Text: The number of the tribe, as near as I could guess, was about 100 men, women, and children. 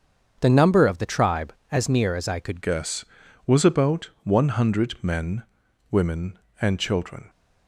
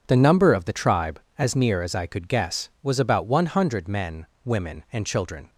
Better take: second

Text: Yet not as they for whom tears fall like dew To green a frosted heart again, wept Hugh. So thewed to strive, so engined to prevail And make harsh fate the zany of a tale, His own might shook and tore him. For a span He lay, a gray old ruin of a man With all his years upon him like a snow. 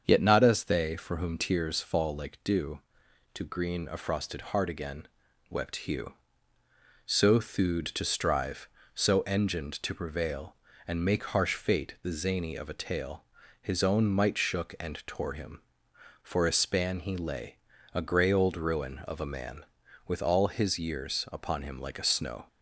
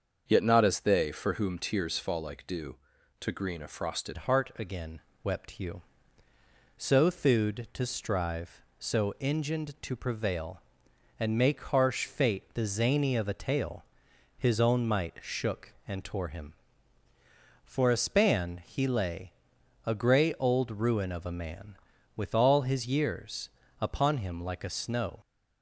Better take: first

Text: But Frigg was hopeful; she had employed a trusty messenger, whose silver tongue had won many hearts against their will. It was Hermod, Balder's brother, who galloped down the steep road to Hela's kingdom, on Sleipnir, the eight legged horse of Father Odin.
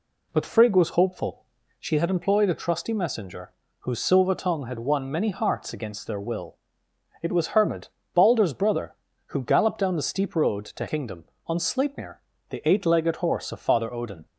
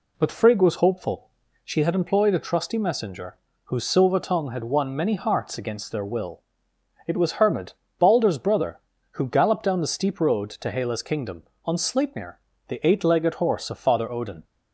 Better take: second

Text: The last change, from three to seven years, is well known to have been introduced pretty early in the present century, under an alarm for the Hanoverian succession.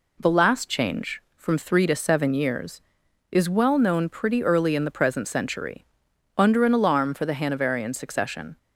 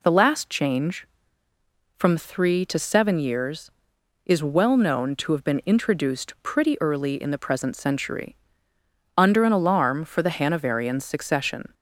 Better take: second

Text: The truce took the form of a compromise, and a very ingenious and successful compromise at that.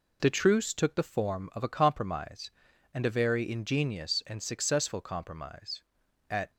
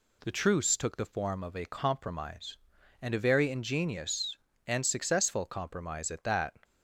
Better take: second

